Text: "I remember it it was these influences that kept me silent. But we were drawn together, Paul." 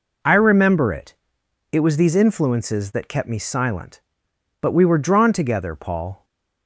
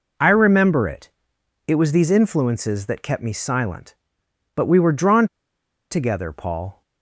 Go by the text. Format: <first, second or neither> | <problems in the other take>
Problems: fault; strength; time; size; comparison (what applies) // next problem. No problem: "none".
first | pauses between "it" and "it"; noticeable; at 1.1 s; 0.56 s long; noticeable in the first // pauses between "drawn" and "together"; noticeable; at 5.2 s; 0.64 s long